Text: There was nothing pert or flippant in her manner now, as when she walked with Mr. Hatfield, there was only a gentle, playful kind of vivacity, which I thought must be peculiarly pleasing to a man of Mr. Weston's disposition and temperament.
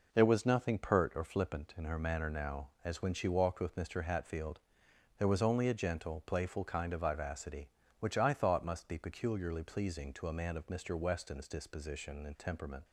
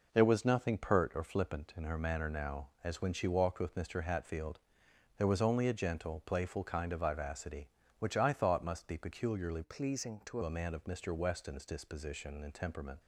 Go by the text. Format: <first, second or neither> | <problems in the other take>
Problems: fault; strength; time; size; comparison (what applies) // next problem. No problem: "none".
first | changes voice from "pleasing" to "to"; from 9.6 to 10.4 s; 0.8 s long